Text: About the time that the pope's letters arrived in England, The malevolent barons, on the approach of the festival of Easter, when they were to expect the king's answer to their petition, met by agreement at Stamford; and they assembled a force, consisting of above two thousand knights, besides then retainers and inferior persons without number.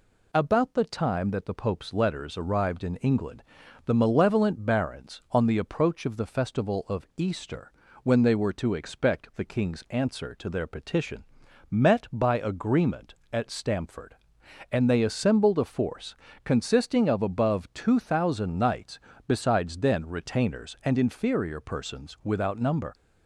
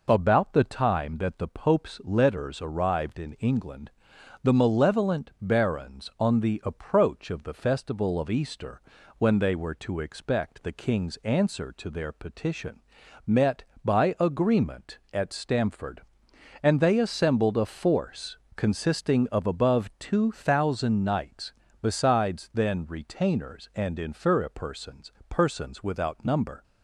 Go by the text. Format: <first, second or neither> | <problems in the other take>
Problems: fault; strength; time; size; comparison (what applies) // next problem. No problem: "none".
first | says "persons" twice; at 25.2 s